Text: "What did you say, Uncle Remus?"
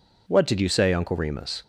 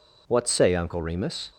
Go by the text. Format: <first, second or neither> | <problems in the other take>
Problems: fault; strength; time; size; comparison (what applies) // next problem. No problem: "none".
first | skips "did you"; at 0.4 s